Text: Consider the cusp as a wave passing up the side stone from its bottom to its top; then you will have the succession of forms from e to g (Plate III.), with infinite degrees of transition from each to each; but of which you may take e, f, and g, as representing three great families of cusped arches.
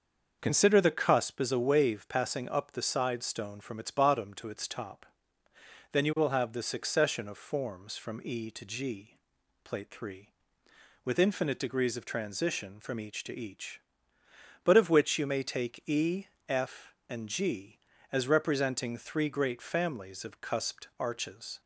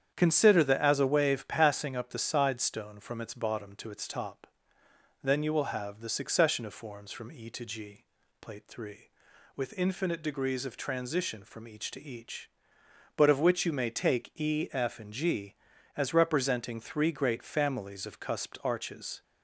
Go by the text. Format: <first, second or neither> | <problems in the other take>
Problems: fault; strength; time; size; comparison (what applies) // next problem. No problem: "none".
first | starts louder than the rest; strong; until 1.1 s; 8.5 dB; also in the first // skips "cusp"; at 0.8 s